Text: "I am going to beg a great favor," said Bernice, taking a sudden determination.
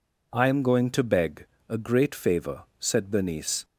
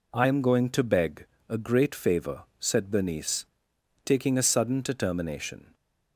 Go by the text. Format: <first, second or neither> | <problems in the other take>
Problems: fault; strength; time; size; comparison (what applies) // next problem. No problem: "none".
second | pauses between "beg" and "a"; slight; at 1.4 s; 0.24 s long; slight in the second // stops before "taking a sudden determination"; at 3.6 s